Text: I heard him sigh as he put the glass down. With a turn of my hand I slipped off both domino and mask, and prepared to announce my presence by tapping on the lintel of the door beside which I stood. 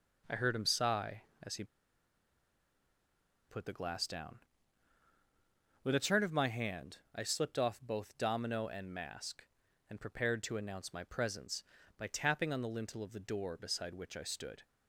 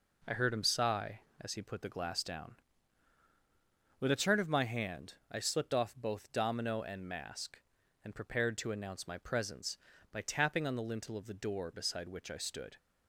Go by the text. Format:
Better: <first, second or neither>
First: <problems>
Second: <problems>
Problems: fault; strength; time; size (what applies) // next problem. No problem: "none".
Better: second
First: pauses between "he" and "put"; strong; at 1.6 s; 1.8 s long // pauses between "hand" and "I"; slight; at 6.9 s; 0.16 s long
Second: pauses between "hand" and "I"; slight; at 5.1 s; 0.16 s long